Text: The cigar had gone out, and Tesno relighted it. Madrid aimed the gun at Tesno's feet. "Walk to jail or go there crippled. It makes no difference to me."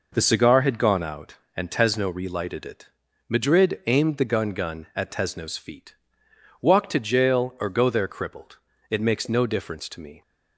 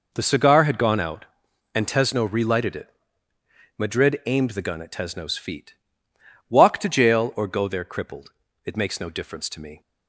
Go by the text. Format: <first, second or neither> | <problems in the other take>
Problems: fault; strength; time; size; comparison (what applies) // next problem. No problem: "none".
second | says "gun" twice; at 4.5 s